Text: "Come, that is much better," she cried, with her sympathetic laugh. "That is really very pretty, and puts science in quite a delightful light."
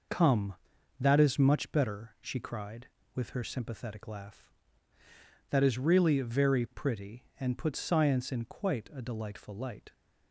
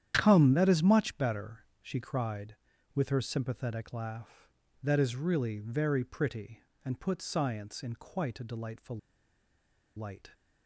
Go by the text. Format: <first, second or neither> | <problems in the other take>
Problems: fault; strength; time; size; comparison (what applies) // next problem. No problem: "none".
first | starts louder than the rest; strong; until 1.1 s; 10 dB // pauses between "delightful" and "light"; at 8.9 s; 0.98 s long